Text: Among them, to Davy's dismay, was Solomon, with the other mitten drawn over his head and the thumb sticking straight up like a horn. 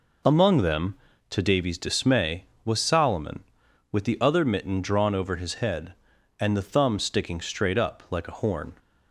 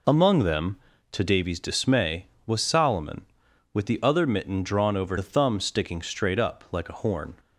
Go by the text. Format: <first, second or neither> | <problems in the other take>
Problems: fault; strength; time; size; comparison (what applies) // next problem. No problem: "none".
first | skips "his head and"; at 5.1 s